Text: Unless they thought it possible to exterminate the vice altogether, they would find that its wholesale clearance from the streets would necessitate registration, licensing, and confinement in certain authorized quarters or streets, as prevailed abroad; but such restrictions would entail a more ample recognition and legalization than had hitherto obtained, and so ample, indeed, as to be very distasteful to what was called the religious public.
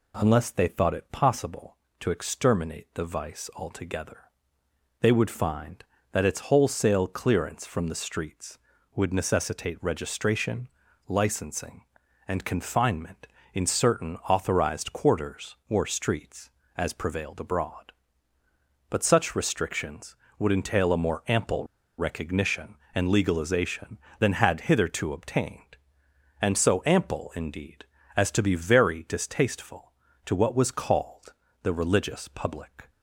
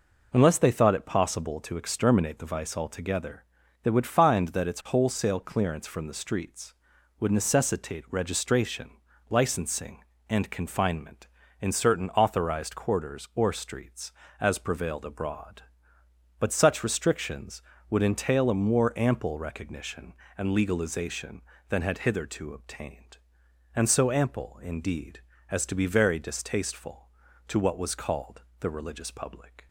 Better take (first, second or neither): second